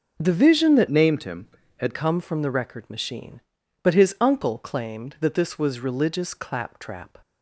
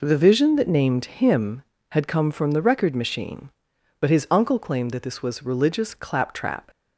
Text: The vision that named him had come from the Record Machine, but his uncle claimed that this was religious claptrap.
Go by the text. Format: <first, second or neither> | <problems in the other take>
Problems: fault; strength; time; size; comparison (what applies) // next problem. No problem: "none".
second | changes voice from "named" to "had"; from 0.8 to 1.9 s; 1.1 s long